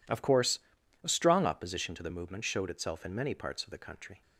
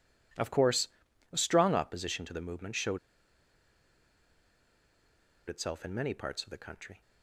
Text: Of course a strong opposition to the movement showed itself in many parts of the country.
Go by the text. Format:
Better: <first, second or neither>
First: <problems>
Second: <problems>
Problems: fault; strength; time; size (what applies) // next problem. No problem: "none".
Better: first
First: pauses between "course" and "a"; at 0.5 s; 0.42 s long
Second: pauses between "course" and "a"; at 0.8 s; 0.42 s long // pauses between "showed" and "itself"; strong; at 2.9 s; 2.5 s long